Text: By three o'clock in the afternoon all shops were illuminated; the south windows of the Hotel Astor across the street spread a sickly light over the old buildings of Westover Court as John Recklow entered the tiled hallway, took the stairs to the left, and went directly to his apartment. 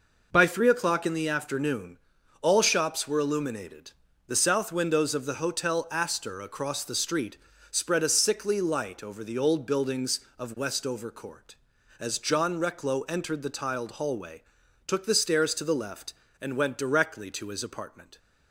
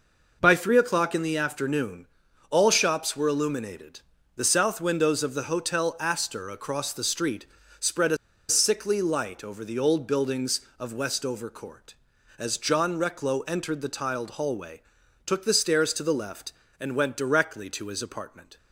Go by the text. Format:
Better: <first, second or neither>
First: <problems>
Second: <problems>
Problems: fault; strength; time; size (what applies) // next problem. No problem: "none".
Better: first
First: pauses between "afternoon" and "all"; at 1.9 s; 0.42 s long // pauses between "street" and "spread"; slight; at 7.3 s; 0.36 s long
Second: pauses between "afternoon" and "all"; at 2.0 s; 0.42 s long // pauses between "street" and "spread"; slight; at 7.4 s; 0.36 s long // pauses between "a" and "sickly"; slight; at 8.1 s; 0.32 s long